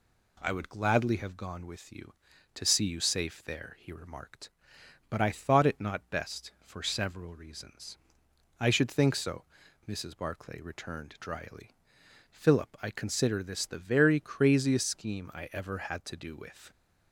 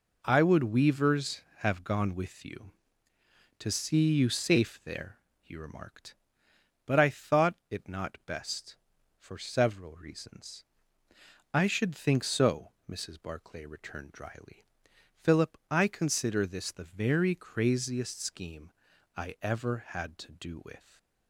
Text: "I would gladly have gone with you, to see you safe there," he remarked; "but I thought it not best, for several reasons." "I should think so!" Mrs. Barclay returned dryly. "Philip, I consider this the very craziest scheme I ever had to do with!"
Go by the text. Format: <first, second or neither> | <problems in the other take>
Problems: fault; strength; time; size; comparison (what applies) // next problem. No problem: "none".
first | says "weavers" for "gladly"; at 0.6 s // pauses between "scheme" and "I"; at 18.7 s; 0.44 s long // stays silent after the last word; slight; from 20.7 s on; 0.5 s long